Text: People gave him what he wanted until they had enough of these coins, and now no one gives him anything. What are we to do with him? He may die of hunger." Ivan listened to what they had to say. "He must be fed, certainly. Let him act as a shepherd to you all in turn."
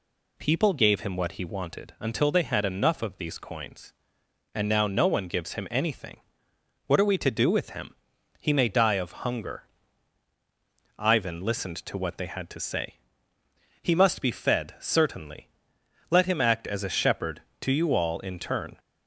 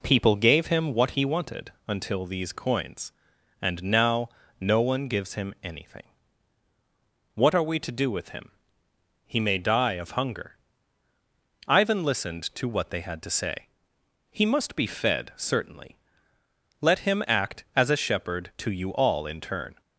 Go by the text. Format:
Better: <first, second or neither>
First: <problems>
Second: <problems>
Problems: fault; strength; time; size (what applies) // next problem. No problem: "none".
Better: first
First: none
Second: pauses between "wanted" and "until"; slight; at 1.7 s; 0.16 s long // skips "they had enough of"; at 2.2 s // pauses between "now" and "no"; slight; at 4.2 s; 0.30 s long